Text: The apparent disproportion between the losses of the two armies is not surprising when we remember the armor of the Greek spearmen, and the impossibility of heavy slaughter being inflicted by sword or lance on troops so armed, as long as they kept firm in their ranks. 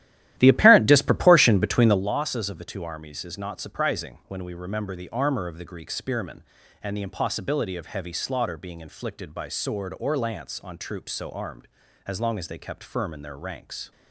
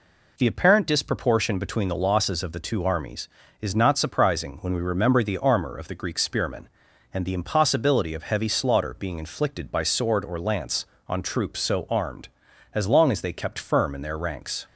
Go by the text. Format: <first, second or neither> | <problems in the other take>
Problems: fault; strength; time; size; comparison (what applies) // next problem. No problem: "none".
second | starts louder than the rest; strong; until 2.0 s; 13.5 dB